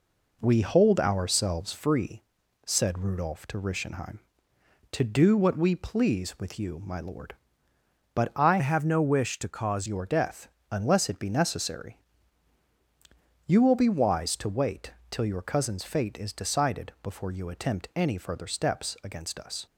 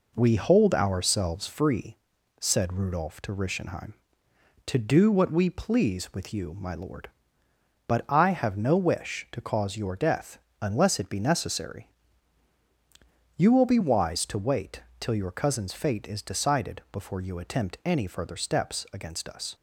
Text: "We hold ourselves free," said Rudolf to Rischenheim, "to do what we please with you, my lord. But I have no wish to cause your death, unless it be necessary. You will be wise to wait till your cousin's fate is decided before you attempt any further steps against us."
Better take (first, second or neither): second